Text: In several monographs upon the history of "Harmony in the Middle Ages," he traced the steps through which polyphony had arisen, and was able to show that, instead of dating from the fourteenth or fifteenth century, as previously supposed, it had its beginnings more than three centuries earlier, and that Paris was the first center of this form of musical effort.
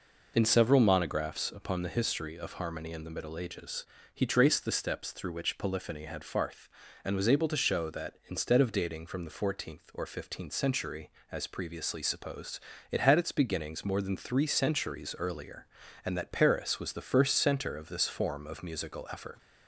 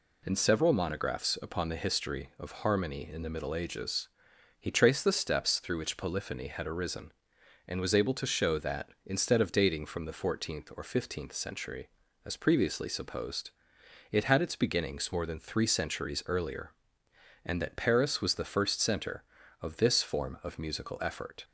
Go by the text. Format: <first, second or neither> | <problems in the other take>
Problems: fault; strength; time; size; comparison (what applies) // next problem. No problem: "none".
second | says "farth" for "arisen"; at 6.2 s